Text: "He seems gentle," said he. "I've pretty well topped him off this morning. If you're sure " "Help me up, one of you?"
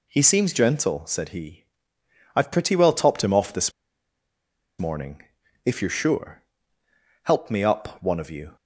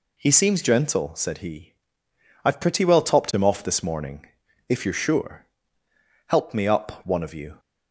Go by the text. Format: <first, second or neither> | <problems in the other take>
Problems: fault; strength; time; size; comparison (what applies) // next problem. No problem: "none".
second | pauses between "this" and "morning"; at 3.7 s; 1.0 s long